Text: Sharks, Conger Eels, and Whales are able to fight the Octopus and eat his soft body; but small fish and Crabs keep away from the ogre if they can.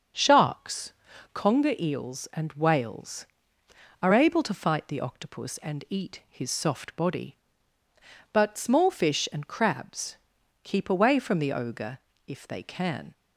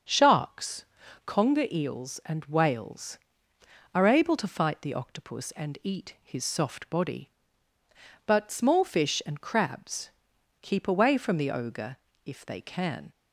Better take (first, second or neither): neither